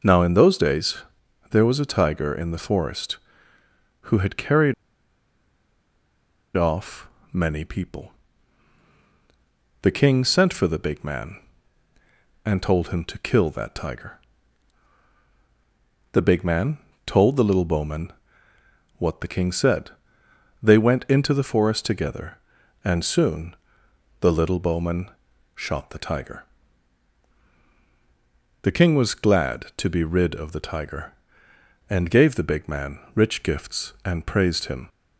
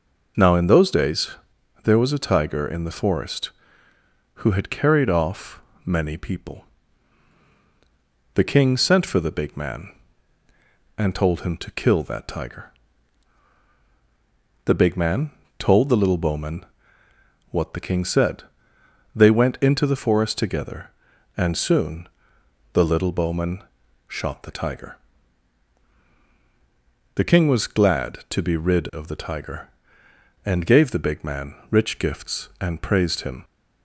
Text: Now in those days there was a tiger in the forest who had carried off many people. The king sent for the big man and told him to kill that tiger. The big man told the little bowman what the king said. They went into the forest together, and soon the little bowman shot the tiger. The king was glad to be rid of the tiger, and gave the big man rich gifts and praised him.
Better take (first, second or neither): second